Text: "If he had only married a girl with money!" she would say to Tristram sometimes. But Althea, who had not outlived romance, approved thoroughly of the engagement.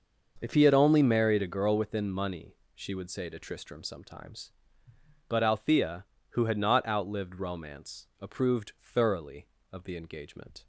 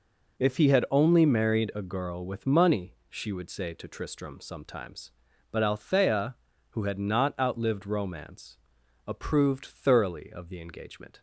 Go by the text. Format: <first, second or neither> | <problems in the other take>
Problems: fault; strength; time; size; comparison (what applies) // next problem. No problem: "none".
second | starts louder than the rest; noticeable; until 1.4 s; 6 dB // says "within" for "with"; at 1.7 s